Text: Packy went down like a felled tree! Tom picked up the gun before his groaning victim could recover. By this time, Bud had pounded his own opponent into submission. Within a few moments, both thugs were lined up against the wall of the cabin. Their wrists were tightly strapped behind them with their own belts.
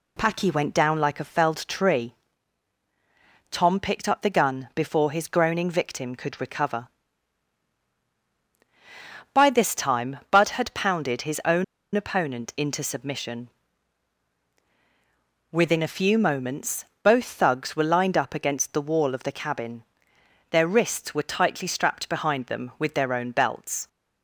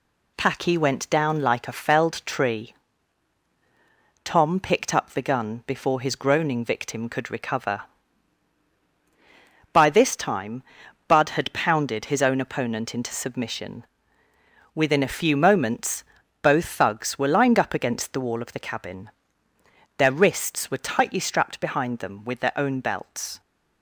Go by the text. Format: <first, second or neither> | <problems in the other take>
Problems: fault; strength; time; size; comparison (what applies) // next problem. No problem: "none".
second | pauses between "own" and "opponent"; slight; at 11.6 s; 0.31 s long